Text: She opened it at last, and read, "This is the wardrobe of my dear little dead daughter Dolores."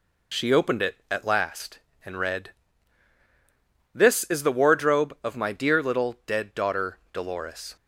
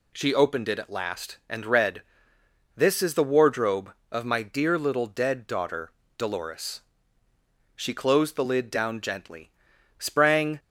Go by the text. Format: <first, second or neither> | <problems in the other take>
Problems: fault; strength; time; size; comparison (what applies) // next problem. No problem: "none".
first | pauses between "daughter" and "Dolores"; slight; at 5.8 s; 0.28 s long; slight in the first // goes on to say "She closed the lid down gently sprang"; strong; from 7.7 s on; 2.8 s long